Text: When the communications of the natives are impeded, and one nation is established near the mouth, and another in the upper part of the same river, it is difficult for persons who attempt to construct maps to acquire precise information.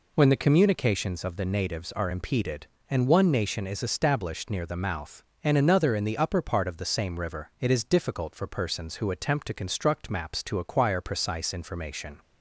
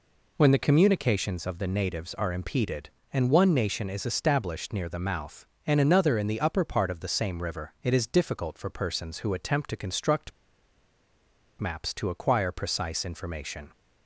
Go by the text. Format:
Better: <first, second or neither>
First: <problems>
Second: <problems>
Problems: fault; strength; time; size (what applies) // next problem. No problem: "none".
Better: first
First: none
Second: pauses between "construct" and "maps"; strong; at 10.3 s; 1.2 s long